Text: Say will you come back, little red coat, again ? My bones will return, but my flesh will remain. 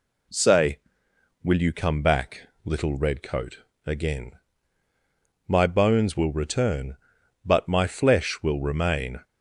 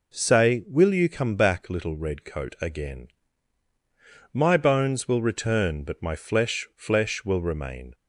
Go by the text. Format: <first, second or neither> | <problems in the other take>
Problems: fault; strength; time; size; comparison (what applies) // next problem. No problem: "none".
first | says "flesh" twice; at 6.7 s